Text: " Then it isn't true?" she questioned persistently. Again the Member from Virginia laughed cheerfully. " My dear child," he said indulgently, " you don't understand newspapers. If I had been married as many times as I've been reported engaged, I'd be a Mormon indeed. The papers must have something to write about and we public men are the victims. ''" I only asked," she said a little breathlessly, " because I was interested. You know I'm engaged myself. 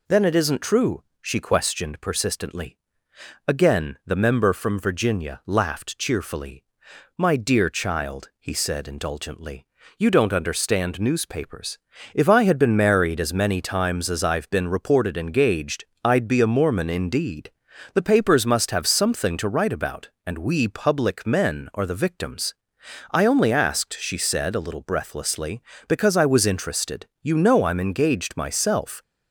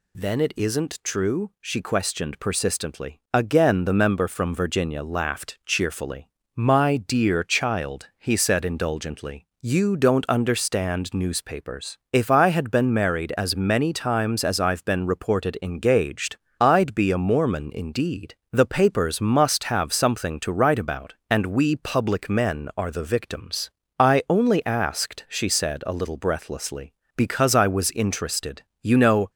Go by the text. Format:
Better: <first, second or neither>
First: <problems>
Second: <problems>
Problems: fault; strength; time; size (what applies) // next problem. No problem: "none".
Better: first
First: none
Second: stops before "I'm engaged myself"; at 29.2 s